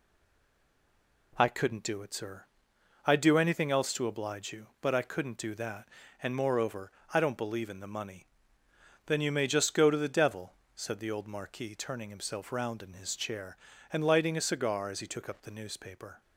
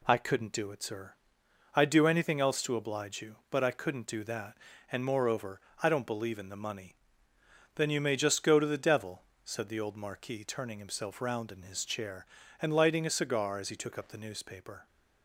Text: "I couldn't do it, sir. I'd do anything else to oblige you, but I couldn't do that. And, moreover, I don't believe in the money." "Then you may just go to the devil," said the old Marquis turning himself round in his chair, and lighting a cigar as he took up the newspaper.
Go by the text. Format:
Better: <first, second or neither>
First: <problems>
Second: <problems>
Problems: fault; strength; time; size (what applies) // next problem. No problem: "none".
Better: second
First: stays silent before the first word; noticeable; until 1.3 s; 1.3 s long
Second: none